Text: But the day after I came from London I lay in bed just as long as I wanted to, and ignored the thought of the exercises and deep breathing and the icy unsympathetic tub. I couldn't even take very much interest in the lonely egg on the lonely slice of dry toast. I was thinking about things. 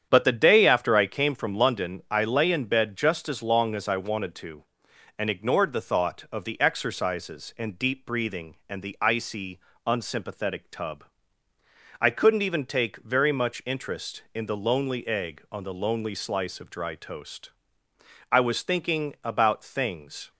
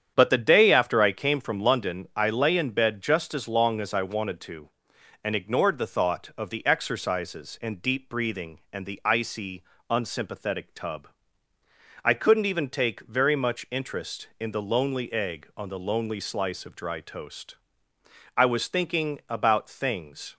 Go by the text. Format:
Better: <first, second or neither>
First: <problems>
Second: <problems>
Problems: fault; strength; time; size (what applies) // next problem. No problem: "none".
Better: neither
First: starts louder than the rest; strong; until 1.1 s; 8.5 dB // pauses between "icy" and "unsympathetic"; slight; at 9.5 s; 0.28 s long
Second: starts louder than the rest; strong; until 1.1 s; 8.5 dB // pauses between "icy" and "unsympathetic"; slight; at 9.6 s; 0.28 s long